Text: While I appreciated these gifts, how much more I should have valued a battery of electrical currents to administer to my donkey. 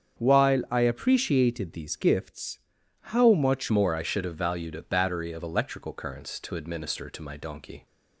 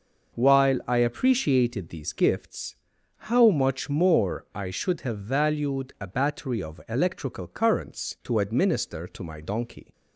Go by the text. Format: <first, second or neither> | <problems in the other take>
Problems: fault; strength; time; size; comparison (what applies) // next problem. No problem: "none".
second | starts louder than the rest; strong; until 1.2 s; 7.5 dB // changes voice at "more"; from 3.6 s on; 4.2 s long